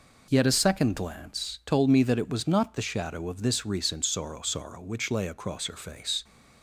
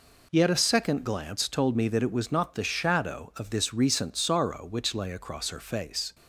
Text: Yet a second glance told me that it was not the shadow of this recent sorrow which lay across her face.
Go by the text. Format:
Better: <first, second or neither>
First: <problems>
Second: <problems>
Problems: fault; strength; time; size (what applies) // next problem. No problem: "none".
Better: second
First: says "sorrow" twice; at 4.4 s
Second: none